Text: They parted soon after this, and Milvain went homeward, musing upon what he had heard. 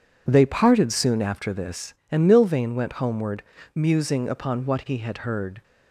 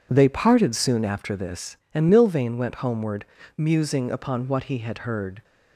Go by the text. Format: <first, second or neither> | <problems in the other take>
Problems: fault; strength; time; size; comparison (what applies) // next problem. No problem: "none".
neither | none